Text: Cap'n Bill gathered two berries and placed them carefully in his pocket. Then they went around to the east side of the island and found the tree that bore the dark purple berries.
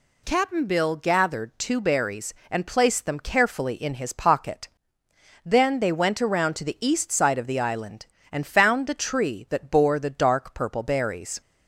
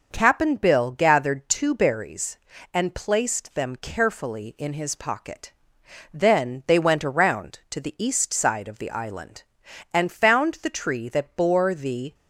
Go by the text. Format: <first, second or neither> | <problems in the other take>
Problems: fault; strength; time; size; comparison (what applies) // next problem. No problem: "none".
first | stops before "dark purple berries"; at 12.1 s